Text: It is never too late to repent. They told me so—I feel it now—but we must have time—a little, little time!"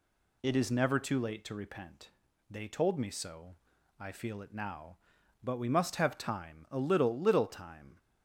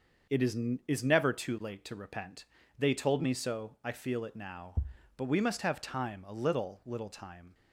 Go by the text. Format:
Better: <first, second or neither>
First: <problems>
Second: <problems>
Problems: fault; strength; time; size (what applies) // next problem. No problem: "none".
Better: first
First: none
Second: starts louder than the rest; until 1.6 s; 6 dB // says "is" twice; at 0.8 s